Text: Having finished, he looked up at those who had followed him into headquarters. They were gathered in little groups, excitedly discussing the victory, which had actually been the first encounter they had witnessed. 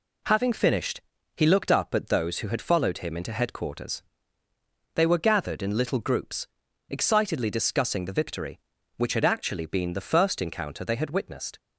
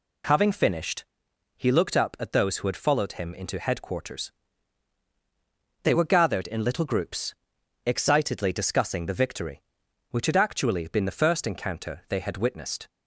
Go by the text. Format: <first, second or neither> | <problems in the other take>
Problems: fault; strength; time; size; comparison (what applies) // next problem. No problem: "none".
neither | none